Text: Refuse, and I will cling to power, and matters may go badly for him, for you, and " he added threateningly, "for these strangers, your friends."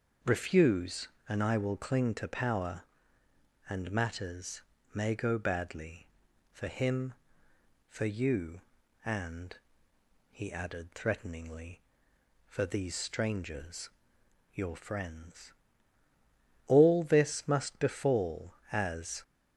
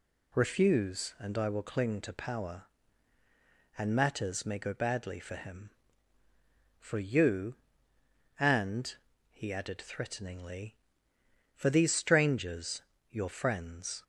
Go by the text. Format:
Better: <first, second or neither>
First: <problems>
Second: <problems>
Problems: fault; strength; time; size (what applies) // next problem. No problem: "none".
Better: second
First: starts louder than the rest; until 1.4 s; 6 dB // pauses between "matters" and "may"; slight; at 4.6 s; 0.32 s long // goes on to say "All this must befall as"; strong; from 16.6 s on; 2.5 s long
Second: none